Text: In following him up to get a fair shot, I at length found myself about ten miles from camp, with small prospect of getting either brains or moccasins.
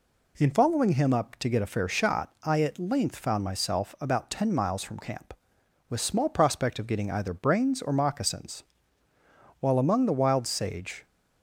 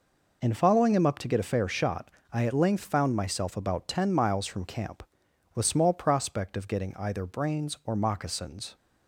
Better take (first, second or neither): second